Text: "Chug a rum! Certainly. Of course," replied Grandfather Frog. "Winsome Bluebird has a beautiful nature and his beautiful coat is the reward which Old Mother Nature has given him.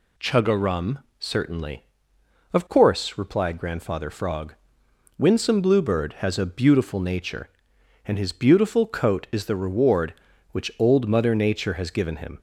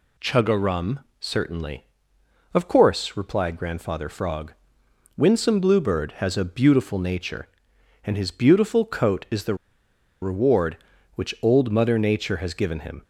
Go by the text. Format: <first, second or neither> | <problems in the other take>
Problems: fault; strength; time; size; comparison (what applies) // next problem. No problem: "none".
first | pauses between "the" and "reward"; noticeable; at 9.5 s; 0.66 s long